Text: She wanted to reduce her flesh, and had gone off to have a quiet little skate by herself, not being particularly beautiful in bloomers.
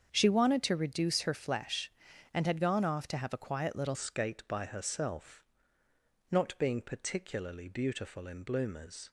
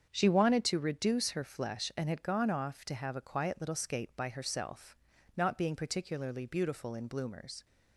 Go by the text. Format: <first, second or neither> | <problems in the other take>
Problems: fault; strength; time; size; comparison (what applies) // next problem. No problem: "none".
second | starts louder than the rest; strong; until 1.1 s; 7 dB; strong in the second // changes voice at "skate"; from 3.9 s on; 5.2 s long